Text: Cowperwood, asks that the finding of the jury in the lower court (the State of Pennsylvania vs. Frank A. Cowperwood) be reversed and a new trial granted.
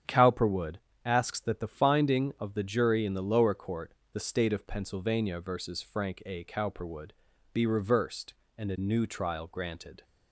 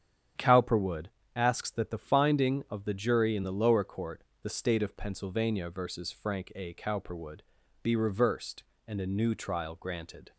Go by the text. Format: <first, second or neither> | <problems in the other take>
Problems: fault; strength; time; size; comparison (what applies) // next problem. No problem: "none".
neither | starts louder than the rest; strong; the same in both